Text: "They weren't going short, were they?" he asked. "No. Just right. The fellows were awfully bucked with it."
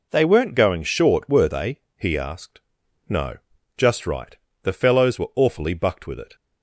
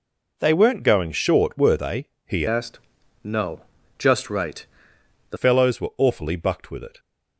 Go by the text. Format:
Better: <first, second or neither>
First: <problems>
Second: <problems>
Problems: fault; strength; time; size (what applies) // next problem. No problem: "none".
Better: first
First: none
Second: changes voice from "asked" to "The"; from 2.4 to 5.3 s; 2.9 s long